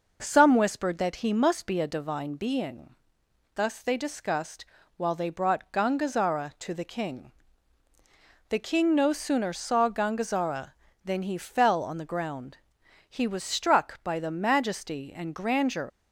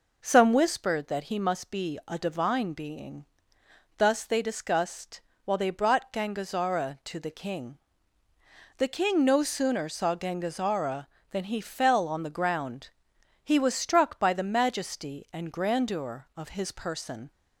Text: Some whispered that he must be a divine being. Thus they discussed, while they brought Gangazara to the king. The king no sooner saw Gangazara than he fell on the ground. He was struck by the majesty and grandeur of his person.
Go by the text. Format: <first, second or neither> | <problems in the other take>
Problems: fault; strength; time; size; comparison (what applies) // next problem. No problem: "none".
second | stops before "of his person"; at 15.8 s